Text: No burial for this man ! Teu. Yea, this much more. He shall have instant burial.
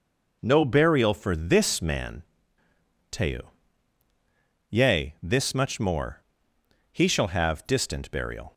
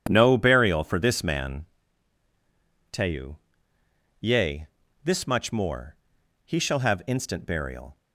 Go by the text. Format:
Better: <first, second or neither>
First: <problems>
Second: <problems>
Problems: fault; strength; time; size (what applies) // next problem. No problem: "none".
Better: second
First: says "distant" for "instant"; at 7.6 s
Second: none